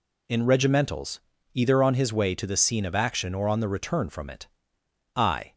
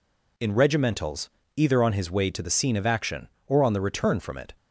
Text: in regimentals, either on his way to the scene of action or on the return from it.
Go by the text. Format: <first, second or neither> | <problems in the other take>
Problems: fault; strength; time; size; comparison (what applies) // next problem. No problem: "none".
second | goes on to say "I"; slight; from 5.1 s on; 0.40 s long